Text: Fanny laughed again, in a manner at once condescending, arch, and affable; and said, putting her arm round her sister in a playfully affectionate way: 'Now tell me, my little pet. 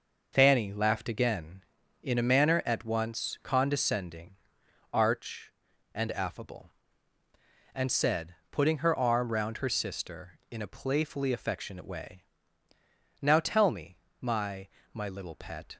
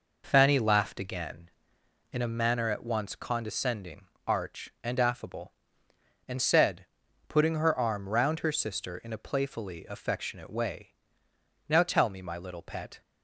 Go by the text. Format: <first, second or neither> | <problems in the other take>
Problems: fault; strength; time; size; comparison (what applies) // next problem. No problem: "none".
second | says "my" twice; at 14.9 s